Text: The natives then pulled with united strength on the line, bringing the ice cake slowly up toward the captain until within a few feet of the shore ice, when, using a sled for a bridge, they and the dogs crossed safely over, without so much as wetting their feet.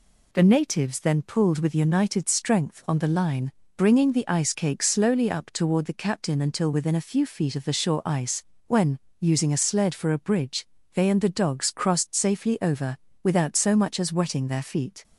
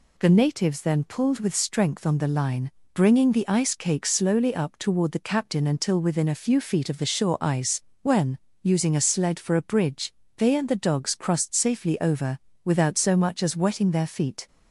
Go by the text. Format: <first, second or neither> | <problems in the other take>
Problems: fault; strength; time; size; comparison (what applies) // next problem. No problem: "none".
first | skips "united"; at 1.5 s